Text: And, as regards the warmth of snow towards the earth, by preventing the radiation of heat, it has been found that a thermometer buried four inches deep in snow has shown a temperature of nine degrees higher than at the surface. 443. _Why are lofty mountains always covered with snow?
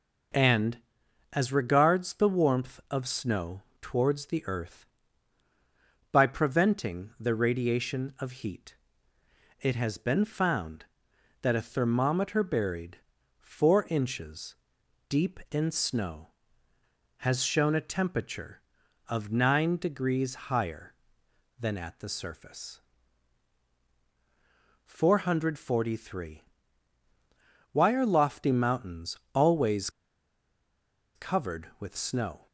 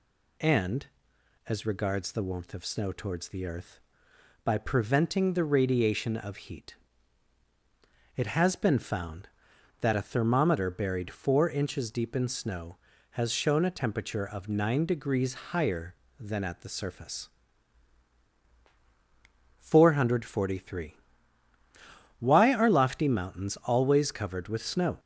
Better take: second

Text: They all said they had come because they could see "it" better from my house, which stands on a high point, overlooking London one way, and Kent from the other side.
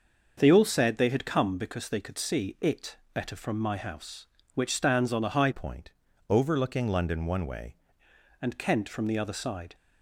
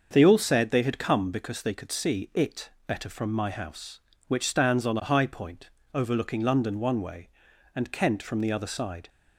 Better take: second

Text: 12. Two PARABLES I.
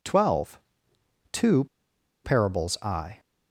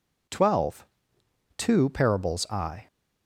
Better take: second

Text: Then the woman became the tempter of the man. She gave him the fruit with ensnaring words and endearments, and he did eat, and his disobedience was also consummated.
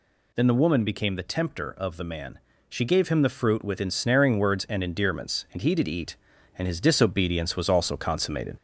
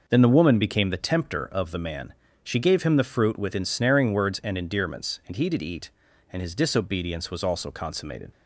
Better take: second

